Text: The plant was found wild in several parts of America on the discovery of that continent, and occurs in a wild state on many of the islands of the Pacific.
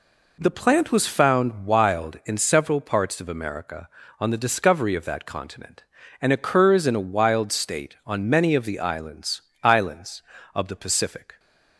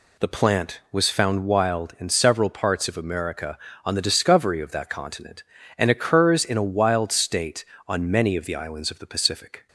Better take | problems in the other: second | says "islands" twice; at 9.6 s

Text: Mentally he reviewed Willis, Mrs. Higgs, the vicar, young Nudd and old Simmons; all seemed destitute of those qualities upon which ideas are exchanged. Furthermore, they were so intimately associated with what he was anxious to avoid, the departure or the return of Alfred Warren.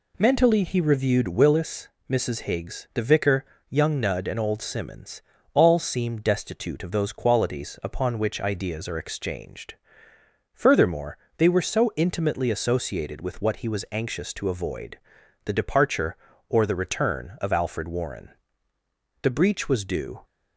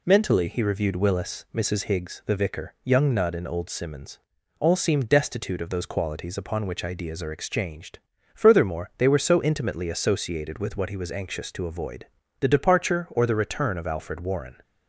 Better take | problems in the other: second | goes on to say "The breach was due"; noticeable; from 19.2 s on; 1.0 s long

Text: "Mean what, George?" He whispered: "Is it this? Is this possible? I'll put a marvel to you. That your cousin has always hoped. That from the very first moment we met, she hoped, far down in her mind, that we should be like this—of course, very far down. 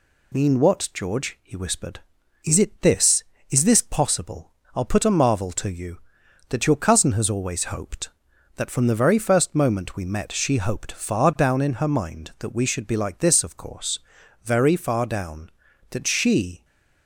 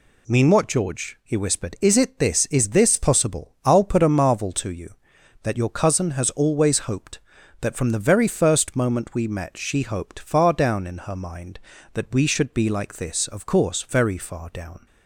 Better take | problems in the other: second | goes on to say "That she"; noticeable; from 15.9 s on; 0.74 s long

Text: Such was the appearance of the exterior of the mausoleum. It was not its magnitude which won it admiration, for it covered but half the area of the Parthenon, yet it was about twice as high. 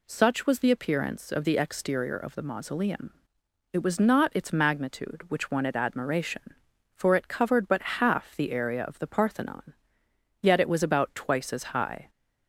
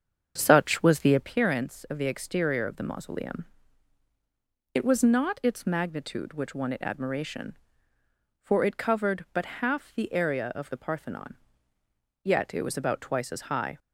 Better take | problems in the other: first | starts louder than the rest; strong; until 1.3 s; 7 dB

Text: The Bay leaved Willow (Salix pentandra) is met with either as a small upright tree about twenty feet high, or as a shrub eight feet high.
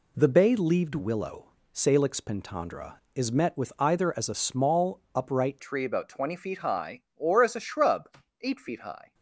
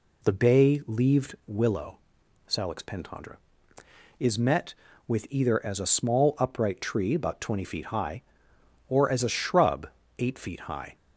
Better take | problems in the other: second | changes voice at "tree"; from 5.5 s on; 3.6 s long // pauses between "shrub" and "eight"; slight; at 8.1 s; 0.24 s long; slight in the second

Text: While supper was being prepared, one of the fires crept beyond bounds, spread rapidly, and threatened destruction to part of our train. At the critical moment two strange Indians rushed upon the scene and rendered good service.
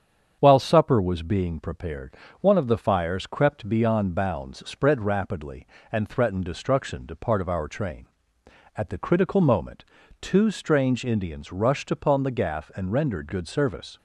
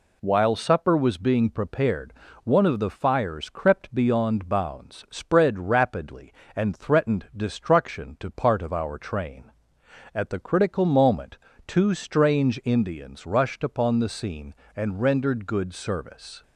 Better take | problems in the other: second | starts louder than the rest; strong; until 1.4 s; 7.5 dB // pauses between "moment" and "two"; at 9.8 s; 0.38 s long; slight in the second // says "gaff" for "scene"; at 12.3 s

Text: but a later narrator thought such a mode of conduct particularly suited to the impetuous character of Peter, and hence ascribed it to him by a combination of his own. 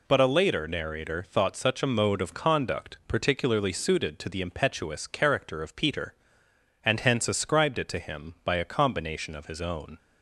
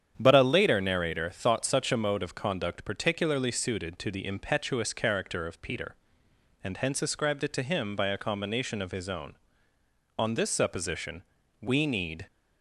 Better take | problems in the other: first | starts louder than the rest; strong; until 1.1 s; 8.5 dB // goes on to say "On this supposition we need"; strong; from 10.1 s on; 2.0 s long

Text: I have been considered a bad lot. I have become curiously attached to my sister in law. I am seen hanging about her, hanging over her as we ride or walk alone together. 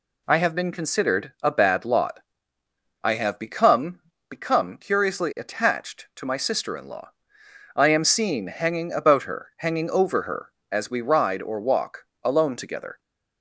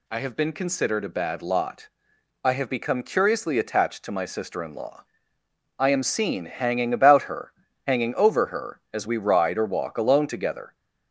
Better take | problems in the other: second | says "become" twice; at 4.2 s // pauses between "walk" and "alone"; slight; at 12.0 s; 0.18 s long

